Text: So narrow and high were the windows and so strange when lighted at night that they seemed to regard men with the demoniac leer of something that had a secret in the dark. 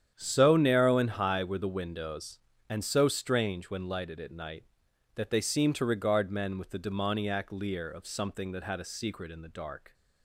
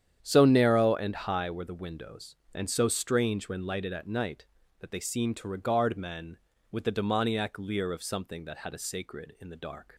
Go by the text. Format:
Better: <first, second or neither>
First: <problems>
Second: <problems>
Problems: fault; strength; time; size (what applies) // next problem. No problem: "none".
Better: first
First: starts louder than the rest; strong; until 1.1 s; 9 dB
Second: starts louder than the rest; strong; until 1.2 s; 9 dB // says "sacred" for "secret"; at 8.7 s